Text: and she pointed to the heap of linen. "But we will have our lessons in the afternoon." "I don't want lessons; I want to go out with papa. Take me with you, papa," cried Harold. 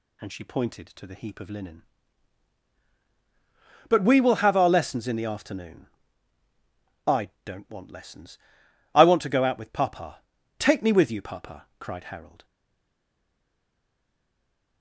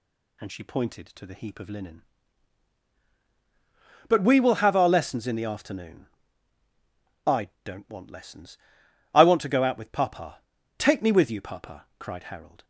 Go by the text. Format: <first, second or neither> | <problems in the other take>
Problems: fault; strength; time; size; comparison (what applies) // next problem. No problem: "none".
second | stays silent after the last word; from 12.4 s on; 2.4 s long